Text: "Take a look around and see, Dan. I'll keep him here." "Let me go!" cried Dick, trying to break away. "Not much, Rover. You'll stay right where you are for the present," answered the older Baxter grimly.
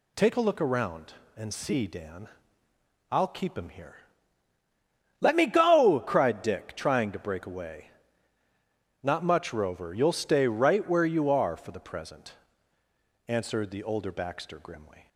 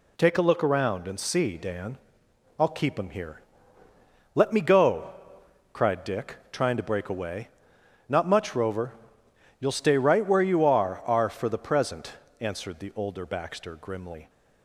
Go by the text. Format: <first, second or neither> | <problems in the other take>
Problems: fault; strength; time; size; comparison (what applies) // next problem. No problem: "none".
first | says "are" twice; at 11.0 s